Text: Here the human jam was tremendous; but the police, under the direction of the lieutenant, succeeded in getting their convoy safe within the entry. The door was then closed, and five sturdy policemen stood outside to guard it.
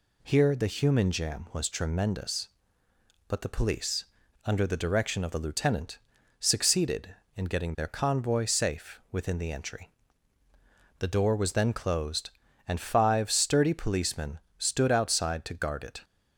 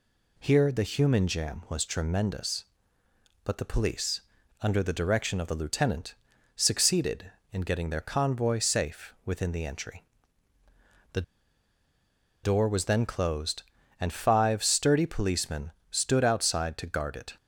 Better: first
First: pauses between "policemen" and "stood"; slight; at 14.3 s; 0.20 s long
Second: pauses between "The" and "door"; at 11.2 s; 1.2 s long // pauses between "policemen" and "stood"; slight; at 15.7 s; 0.20 s long

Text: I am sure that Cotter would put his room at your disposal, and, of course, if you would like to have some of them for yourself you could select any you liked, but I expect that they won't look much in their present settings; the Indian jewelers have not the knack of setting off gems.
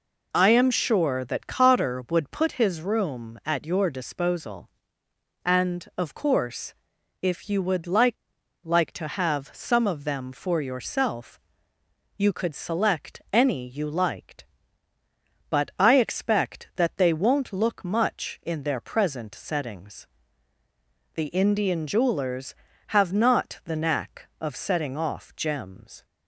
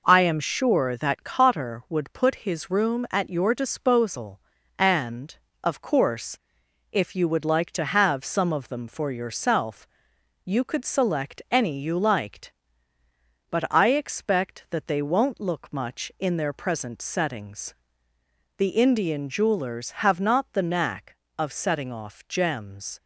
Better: second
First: says "like" twice; at 8.6 s // pauses between "yourself" and "you"; noticeable; at 11.3 s; 0.80 s long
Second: pauses between "yourself" and "you"; noticeable; at 9.8 s; 0.58 s long

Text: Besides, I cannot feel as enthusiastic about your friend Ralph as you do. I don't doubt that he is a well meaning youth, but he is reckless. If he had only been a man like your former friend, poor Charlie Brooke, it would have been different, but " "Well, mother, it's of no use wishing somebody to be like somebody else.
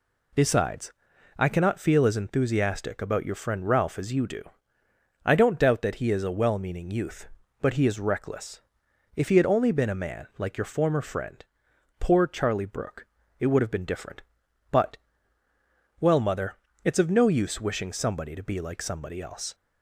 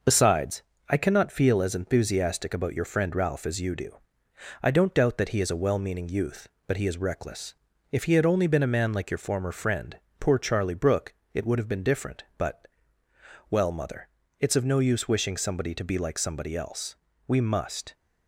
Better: first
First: none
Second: goes on to say "We must"; noticeable; from 17.2 s on; 0.66 s long

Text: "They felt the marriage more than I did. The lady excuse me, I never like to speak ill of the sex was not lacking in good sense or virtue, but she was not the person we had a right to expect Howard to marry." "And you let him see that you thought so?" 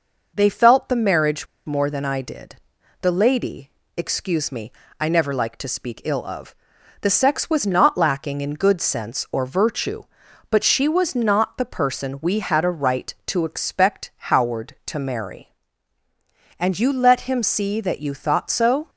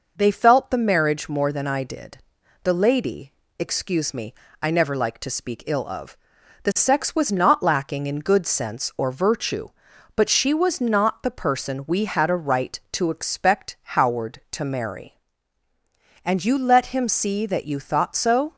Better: second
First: pauses between "marriage" and "more"; slight; at 1.4 s; 0.20 s long // pauses between "lady" and "excuse"; slight; at 3.7 s; 0.24 s long // pauses between "of" and "the"; noticeable; at 6.5 s; 0.48 s long // pauses between "expect" and "Howard"; slight; at 14.1 s; 0.18 s long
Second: pauses between "lady" and "excuse"; slight; at 3.3 s; 0.24 s long // pauses between "of" and "the"; noticeable; at 6.1 s; 0.48 s long // pauses between "expect" and "Howard"; slight; at 13.7 s; 0.18 s long

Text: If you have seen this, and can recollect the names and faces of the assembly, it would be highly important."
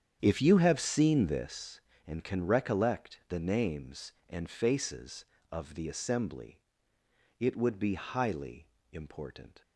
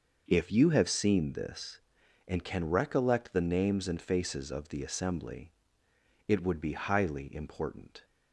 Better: second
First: starts louder than the rest; strong; until 1.5 s; 8.5 dB // pauses between "highly" and "important"; slight; at 8.6 s; 0.24 s long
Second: none

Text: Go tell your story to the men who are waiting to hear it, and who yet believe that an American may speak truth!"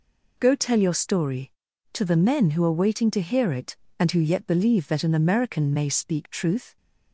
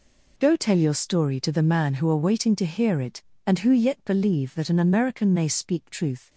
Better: first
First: none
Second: says "man" for "men"; at 1.6 s

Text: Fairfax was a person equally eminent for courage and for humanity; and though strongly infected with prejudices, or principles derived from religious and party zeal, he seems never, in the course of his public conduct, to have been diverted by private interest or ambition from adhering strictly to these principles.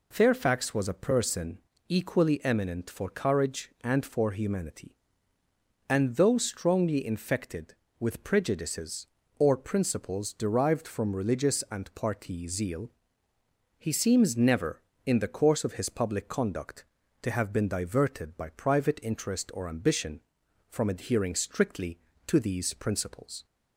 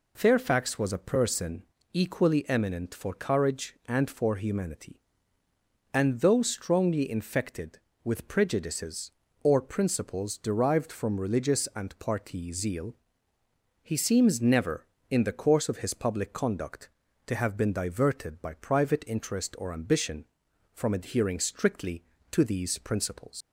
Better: first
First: pauses between "person" and "equally"; slight; at 1.5 s; 0.30 s long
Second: pauses between "person" and "equally"; slight; at 1.6 s; 0.30 s long // leaves "principles" unfinished; at 23.4 s; 95 ms

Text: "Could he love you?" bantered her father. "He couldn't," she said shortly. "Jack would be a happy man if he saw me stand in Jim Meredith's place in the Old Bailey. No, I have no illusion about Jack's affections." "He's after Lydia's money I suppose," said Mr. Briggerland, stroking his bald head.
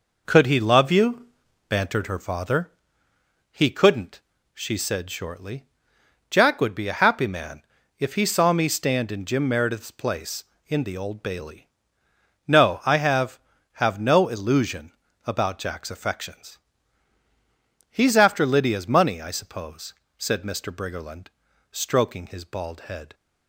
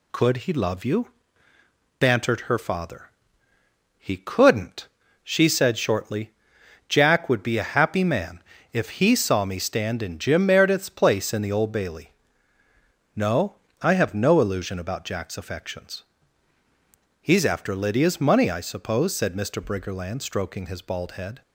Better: second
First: pauses between "man" and "if"; at 7.6 s; 0.38 s long // says "have" twice; at 13.7 s // pauses between "illusion" and "about"; slight; at 14.9 s; 0.34 s long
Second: pauses between "man" and "if"; slight; at 8.4 s; 0.30 s long

